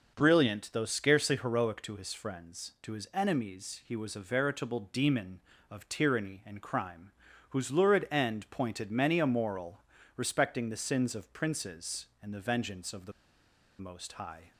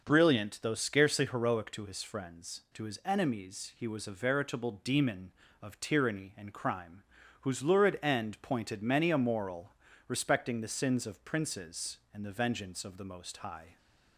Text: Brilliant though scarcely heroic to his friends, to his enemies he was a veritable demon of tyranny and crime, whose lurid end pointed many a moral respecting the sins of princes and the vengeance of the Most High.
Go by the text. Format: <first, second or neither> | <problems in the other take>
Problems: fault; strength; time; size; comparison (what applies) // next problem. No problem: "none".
second | pauses between "moral" and "respecting"; slight; at 9.8 s; 0.34 s long; slight in the second // pauses between "the" and "Most"; noticeable; at 13.1 s; 0.68 s long